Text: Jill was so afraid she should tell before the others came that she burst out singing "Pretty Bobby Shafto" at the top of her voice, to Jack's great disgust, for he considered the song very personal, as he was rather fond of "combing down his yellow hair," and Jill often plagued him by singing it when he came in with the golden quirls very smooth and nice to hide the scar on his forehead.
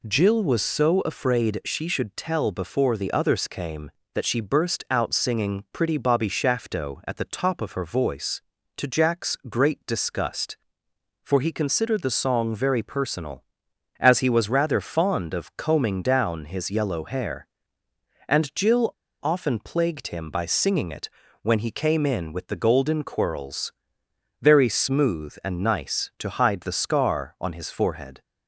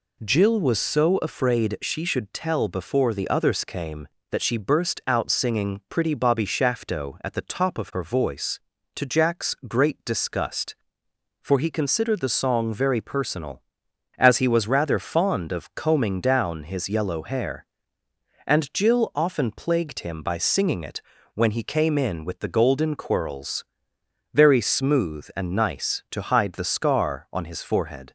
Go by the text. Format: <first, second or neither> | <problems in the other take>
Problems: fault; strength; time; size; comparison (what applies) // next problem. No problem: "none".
second | pauses between "Jill" and "often"; slight; at 18.9 s; 0.30 s long // pauses between "it" and "when"; slight; at 21.0 s; 0.32 s long; slight in the second // pauses between "quirls" and "very"; noticeable; at 23.7 s; 0.68 s long; noticeable in the second